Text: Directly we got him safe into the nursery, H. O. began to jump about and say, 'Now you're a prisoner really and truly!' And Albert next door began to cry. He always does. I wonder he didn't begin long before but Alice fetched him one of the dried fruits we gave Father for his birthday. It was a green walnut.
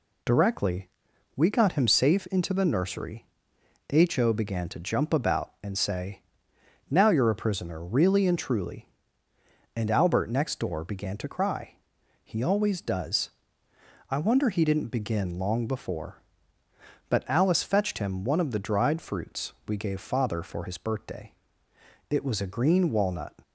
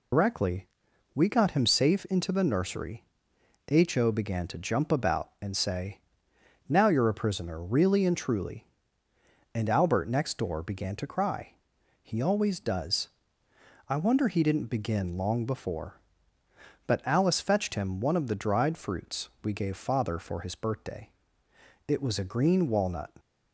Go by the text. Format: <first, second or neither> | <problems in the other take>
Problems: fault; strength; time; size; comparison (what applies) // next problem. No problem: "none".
first | loses the start of "Directly"; at 0.1 s; 100 ms // pauses between "Directly" and "we"; noticeable; at 0.6 s; 0.46 s long; noticeable in the first // pauses between "fruits" and "we"; slight; at 19.2 s; 0.16 s long; slight in the first